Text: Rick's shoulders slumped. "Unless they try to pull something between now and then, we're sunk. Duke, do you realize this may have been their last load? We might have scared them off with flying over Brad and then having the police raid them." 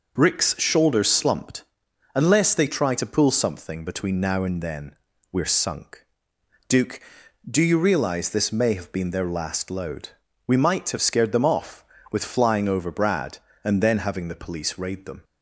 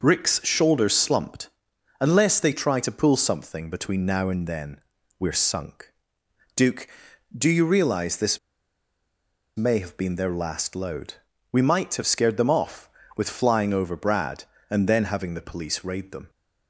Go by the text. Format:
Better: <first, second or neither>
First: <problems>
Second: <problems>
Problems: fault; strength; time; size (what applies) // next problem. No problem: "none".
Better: first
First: none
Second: pauses between "this" and "may"; at 8.3 s; 1.1 s long